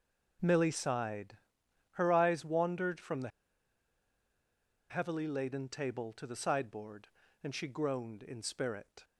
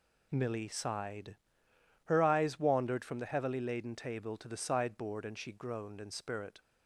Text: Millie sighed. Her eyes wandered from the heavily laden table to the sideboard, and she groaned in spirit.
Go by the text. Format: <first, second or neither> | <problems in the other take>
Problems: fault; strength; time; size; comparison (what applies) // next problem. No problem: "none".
second | pauses between "the" and "heavily"; strong; at 3.2 s; 1.6 s long